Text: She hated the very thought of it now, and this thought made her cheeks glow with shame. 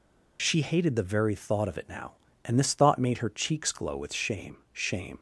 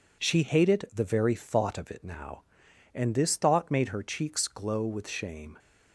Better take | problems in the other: second | says "shame" twice; at 4.7 s

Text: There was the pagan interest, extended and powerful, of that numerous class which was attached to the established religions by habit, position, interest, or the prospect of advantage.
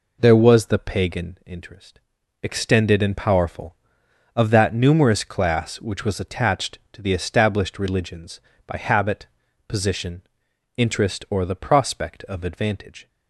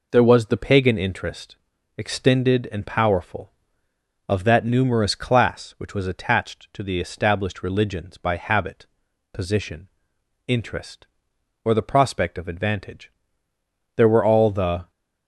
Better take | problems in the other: first | goes on to say "There were all the"; noticeable; from 13.9 s on; 0.94 s long

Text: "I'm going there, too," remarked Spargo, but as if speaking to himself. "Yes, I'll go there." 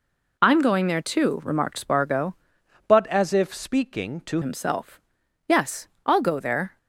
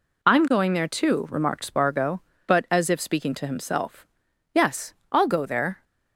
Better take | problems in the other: second | changes voice from "but" to "to"; from 2.8 to 4.4 s; 1.6 s long

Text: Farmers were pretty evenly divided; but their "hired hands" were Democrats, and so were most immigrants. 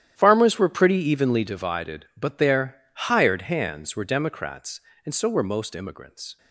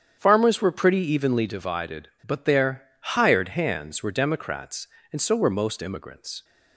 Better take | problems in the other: second | gets quieter; strong; throughout; 14 dB // starts louder than the rest; strong; until 1.1 s; 11 dB; strong in the second // pauses between "their" and "hired"; slight; at 2.7 s; 0.34 s long; slight in the second

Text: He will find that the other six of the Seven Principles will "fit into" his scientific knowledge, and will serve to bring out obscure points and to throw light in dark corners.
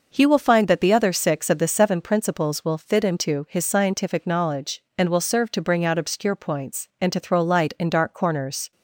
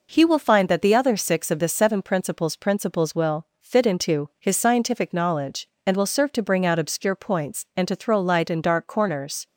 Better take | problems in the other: first | says "Principles" twice; at 2.5 s

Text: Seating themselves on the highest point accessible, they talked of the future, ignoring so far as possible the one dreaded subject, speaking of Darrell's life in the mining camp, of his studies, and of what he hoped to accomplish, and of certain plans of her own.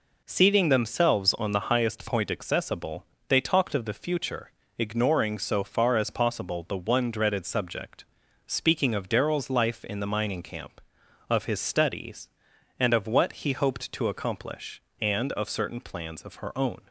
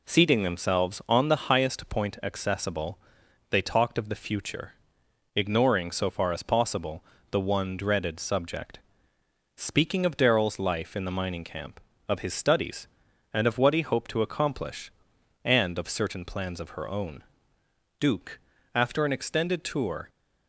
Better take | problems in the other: first | pauses between "possible" and "the"; slight; at 7.0 s; 0.26 s long // goes on to say "Duke after an extended tour"; strong; from 17.9 s on; 2.1 s long

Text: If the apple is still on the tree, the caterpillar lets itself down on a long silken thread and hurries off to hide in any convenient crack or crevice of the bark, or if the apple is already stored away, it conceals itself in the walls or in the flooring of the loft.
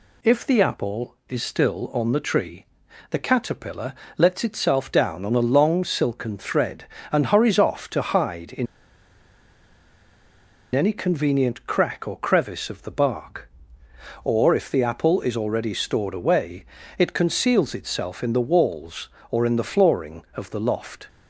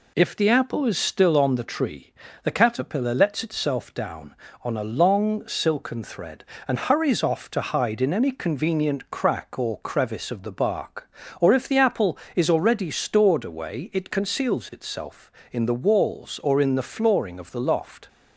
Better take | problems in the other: second | pauses between "caterpillar" and "lets"; slight; at 3.9 s; 0.24 s long // pauses between "in" and "any"; strong; at 8.6 s; 2.0 s long

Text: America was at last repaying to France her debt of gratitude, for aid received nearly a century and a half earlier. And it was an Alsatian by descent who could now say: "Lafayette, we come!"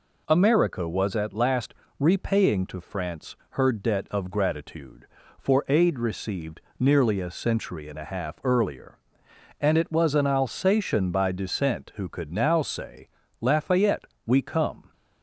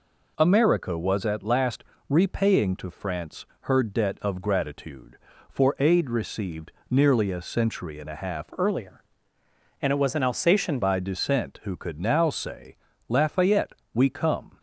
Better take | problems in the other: first | pauses between "last" and "repaying"; slight; at 1.8 s; 0.26 s long; slight in the first // pauses between "France" and "her"; slight; at 3.4 s; 0.16 s long // pauses between "received" and "nearly"; slight; at 6.7 s; 0.18 s long; slight in the first // changes voice from "earlier" to "Alsatian"; from 8.5 to 10.7 s; 2.2 s long

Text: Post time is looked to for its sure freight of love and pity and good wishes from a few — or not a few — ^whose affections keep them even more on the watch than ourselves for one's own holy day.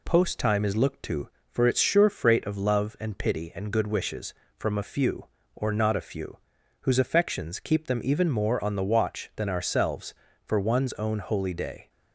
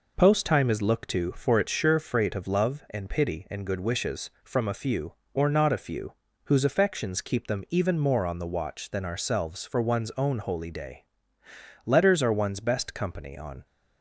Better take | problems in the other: first | goes on to say "Letters are one's best company on"; strong; from 11.8 s on; 1.7 s long

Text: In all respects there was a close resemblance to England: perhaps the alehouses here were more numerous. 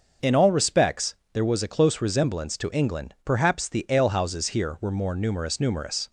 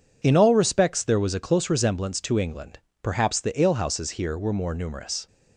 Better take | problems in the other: second | starts louder than the rest; until 1.4 s; 6 dB // pauses between "respects" and "there"; slight; at 1.1 s; 0.18 s long // says "numerous" twice; at 5.5 s

